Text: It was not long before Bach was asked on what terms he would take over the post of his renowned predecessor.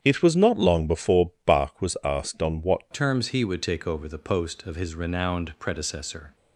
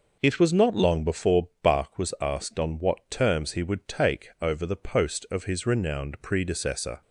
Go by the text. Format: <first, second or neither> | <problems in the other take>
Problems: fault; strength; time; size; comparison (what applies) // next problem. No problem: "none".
second | starts louder than the rest; strong; until 1.0 s; 8.5 dB // changes voice at "terms"; from 2.9 s on; 3.4 s long